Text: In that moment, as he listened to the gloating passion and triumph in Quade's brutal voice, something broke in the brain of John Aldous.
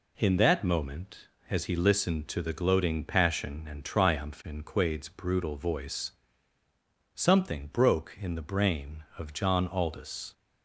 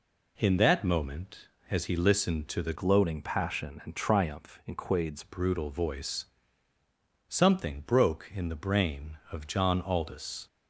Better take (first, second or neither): first